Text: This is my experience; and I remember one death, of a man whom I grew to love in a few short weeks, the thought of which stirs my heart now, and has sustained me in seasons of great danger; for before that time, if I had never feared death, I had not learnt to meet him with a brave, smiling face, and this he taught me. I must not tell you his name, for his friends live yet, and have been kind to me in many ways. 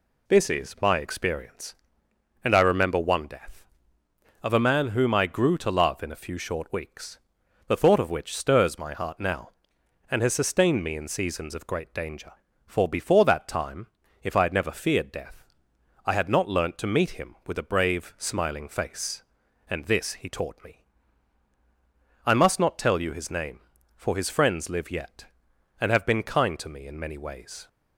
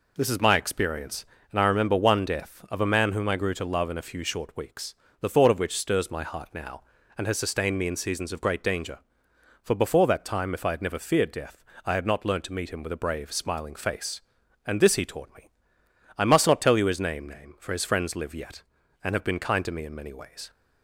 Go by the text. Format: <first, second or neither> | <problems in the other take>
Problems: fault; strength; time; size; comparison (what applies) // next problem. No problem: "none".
first | says "name" twice; at 17.2 s